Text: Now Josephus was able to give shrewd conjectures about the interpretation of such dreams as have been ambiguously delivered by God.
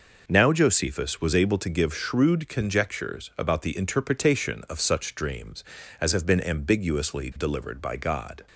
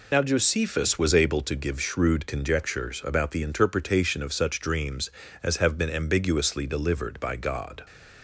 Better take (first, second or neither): first